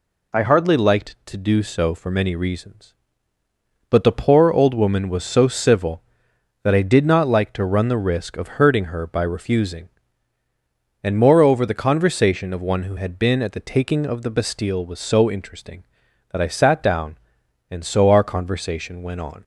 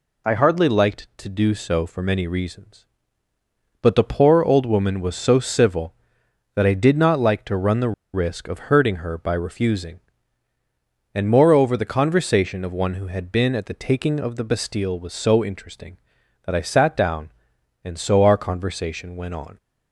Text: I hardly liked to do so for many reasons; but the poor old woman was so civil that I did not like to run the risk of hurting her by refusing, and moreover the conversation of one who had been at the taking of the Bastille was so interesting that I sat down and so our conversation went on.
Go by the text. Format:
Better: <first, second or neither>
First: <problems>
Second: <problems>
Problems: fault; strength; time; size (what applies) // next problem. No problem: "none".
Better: first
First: none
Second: pauses between "the" and "risk"; slight; at 7.9 s; 0.22 s long